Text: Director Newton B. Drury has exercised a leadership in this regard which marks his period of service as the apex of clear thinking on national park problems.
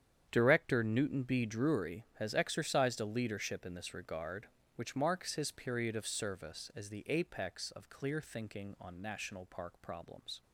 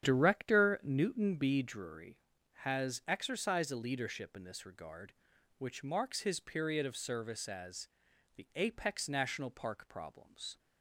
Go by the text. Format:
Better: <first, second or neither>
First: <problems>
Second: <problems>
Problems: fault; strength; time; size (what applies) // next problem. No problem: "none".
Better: first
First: starts louder than the rest; strong; until 1.3 s; 8.5 dB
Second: starts louder than the rest; strong; until 1.0 s; 9 dB // pauses between "as" and "the"; noticeable; at 7.8 s; 0.48 s long // skips "of clear thinking on"; at 9.0 s